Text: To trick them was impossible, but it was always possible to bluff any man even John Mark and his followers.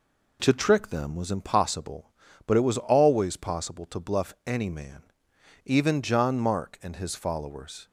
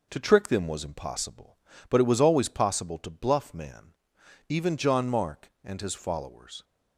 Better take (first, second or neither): first